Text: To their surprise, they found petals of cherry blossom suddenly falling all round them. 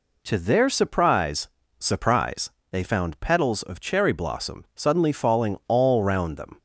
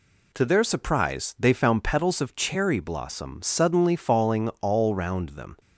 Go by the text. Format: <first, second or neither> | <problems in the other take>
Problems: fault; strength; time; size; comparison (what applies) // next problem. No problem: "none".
second | says "surprise" twice; at 1.7 s